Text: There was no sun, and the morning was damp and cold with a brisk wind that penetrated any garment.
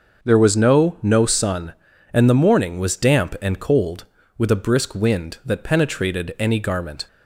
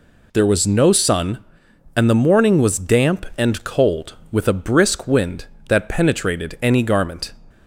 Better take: second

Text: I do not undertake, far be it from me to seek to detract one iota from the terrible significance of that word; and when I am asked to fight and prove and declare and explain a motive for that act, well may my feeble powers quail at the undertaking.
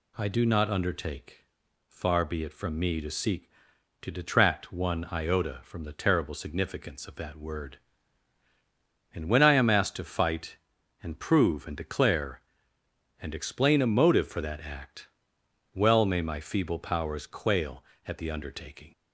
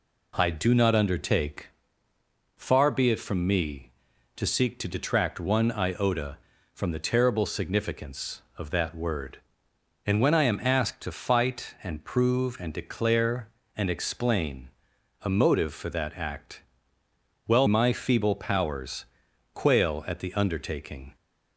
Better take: first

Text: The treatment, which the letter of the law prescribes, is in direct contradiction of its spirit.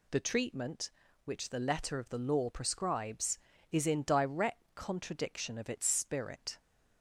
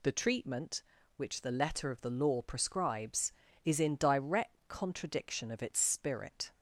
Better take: neither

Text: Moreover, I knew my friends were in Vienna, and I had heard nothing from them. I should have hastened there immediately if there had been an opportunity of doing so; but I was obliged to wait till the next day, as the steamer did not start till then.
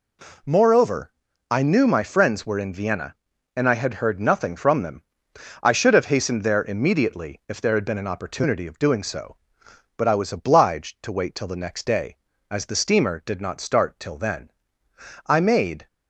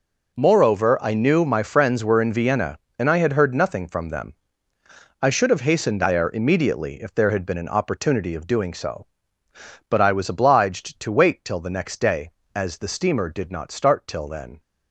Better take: second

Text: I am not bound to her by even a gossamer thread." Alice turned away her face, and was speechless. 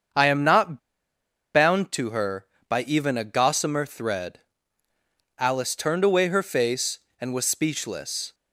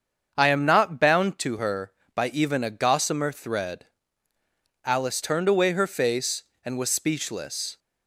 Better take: second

